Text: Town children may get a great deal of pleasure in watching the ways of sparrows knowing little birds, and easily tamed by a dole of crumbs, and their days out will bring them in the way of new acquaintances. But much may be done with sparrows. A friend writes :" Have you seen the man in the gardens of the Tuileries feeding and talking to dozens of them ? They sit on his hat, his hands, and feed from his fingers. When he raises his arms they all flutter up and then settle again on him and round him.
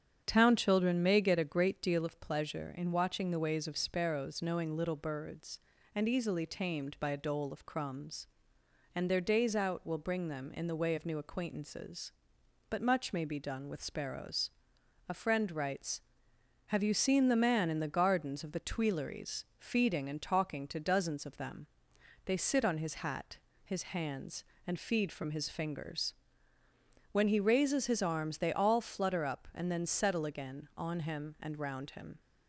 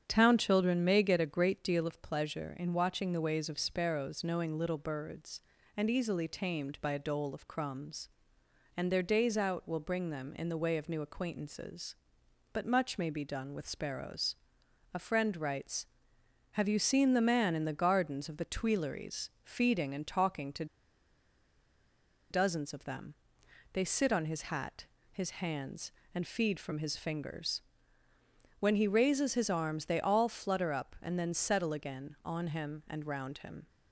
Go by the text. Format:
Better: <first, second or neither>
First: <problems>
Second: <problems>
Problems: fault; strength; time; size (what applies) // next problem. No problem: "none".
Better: first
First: starts louder than the rest; strong; until 1.2 s; 8 dB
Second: starts louder than the rest; strong; until 1.0 s; 8 dB // pauses between "to" and "dozens"; strong; at 20.6 s; 1.6 s long